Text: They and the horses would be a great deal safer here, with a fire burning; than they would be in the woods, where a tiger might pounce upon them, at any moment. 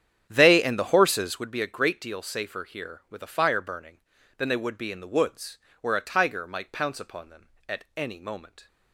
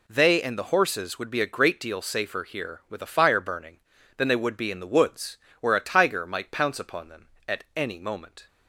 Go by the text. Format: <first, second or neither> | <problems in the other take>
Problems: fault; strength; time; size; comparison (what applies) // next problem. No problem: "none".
second | starts louder than the rest; strong; until 1.6 s; 9 dB